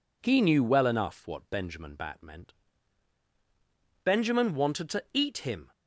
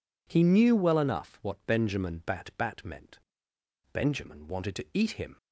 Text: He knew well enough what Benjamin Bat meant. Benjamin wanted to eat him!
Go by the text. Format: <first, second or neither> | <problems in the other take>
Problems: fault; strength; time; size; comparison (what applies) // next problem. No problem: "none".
first | says "Bat" twice; at 2.5 s